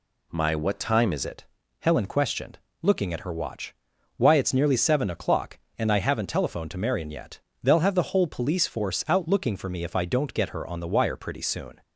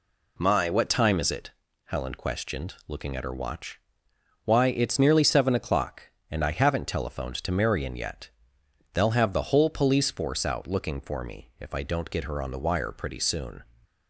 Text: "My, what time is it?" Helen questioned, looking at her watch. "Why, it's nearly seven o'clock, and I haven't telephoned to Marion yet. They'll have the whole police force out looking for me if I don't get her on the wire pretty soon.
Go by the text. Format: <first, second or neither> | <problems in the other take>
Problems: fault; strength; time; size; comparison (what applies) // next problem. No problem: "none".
second | changes voice at "it"; from 1.2 s on; 10.6 s long